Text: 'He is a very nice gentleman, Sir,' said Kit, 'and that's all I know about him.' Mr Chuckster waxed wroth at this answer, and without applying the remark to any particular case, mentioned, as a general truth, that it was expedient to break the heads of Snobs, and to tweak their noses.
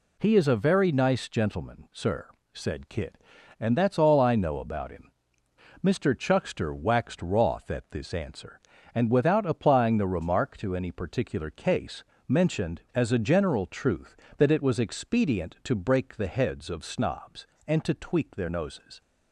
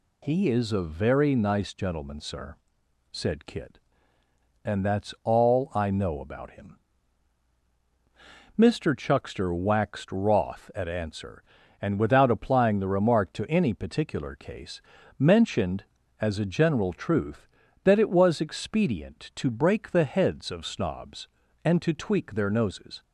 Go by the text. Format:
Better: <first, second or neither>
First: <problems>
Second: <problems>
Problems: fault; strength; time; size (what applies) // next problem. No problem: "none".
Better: first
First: none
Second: skips "this"; at 10.8 s